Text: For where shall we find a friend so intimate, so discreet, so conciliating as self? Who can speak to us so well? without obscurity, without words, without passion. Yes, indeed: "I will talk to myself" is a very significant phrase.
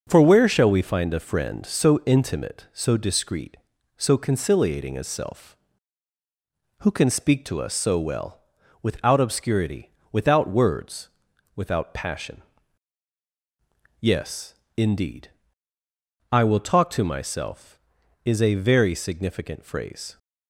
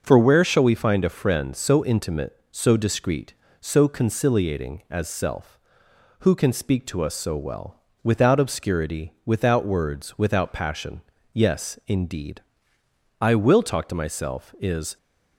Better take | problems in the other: first | starts louder than the rest; until 1.0 s; 6.5 dB // stops before "a very significant phrase"; at 14.9 s

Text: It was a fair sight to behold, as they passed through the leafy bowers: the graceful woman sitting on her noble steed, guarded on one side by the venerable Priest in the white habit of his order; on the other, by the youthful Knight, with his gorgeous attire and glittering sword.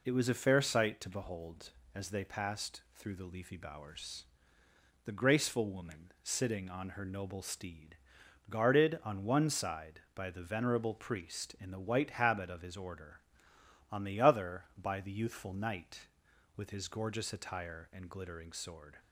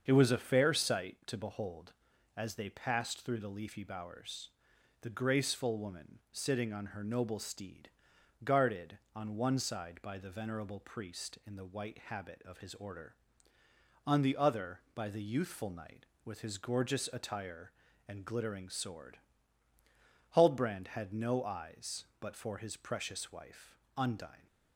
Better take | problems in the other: first | starts louder than the rest; until 1.0 s; 7 dB // goes on to say "Huldbrand had no eyes but for his precious wife Undine"; strong; from 20.3 s on; 4.1 s long

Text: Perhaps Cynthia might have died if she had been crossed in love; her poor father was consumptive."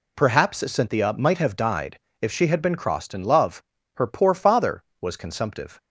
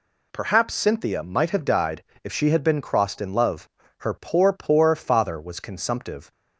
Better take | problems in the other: first | pauses between "died" and "if"; slight; at 2.0 s; 0.20 s long; slight in the first // says "poor" twice; at 4.5 s

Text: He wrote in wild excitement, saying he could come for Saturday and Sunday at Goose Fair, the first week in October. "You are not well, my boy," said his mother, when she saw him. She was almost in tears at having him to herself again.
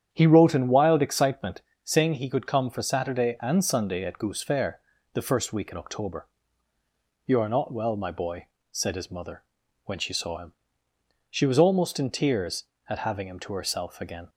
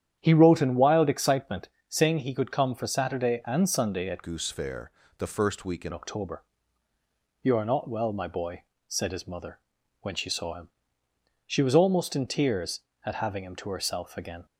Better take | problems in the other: first | starts louder than the rest; strong; until 1.2 s; 9.5 dB; strong in the first // changes voice from "Goose" to "in"; from 4.2 to 5.9 s; 1.7 s long

